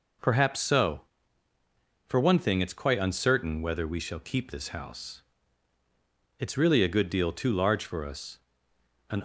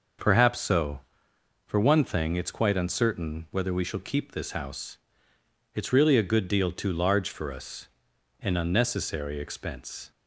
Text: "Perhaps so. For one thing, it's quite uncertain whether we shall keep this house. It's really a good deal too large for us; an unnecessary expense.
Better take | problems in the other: second | stops before "unnecessary expense"; at 9.1 s

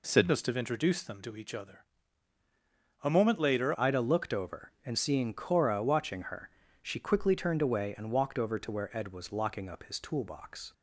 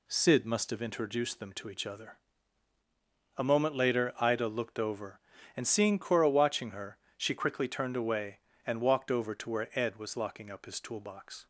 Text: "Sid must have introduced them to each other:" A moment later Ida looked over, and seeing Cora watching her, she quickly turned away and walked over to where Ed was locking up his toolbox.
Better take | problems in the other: second | changes voice at "Ida"; from 3.7 s on; 7.0 s long

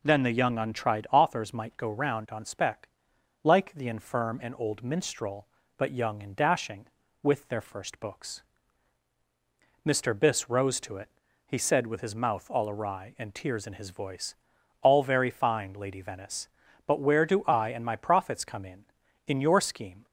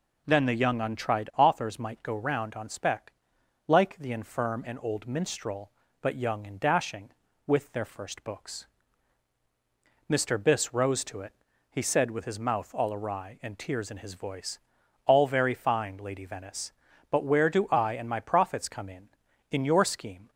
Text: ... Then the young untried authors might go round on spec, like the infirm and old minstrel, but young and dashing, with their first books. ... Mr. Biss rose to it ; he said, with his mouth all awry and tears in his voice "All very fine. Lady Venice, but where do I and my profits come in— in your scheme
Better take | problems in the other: neither | pauses between "voice" and "All"; noticeable; the same in both

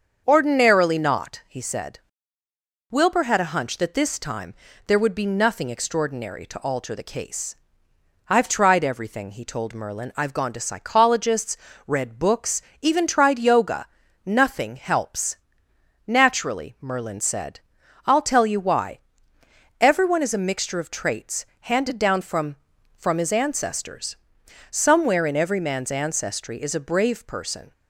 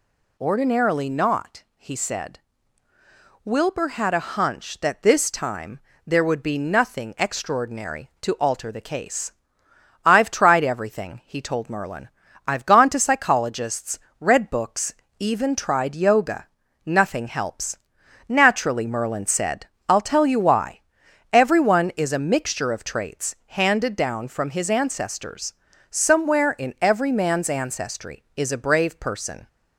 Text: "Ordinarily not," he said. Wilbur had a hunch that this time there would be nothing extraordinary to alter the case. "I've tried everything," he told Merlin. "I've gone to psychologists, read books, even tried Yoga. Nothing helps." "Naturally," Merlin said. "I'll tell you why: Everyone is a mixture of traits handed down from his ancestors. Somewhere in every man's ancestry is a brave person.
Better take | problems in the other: second | starts louder than the rest; until 1.2 s; 7 dB // pauses between "time" and "there"; slight; at 4.5 s; 0.32 s long; slight in the second // pauses between "traits" and "handed"; slight; at 21.4 s; 0.18 s long // says "from" twice; at 22.9 s

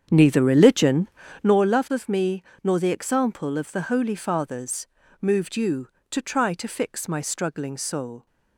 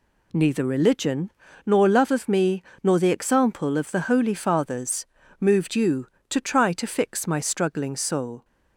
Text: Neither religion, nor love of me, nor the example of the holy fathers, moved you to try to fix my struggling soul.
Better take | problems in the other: second | starts louder than the rest; strong; until 1.6 s; 8 dB

